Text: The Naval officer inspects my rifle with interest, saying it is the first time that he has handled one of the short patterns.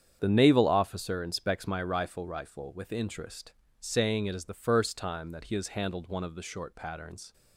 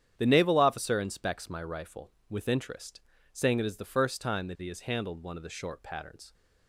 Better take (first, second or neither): second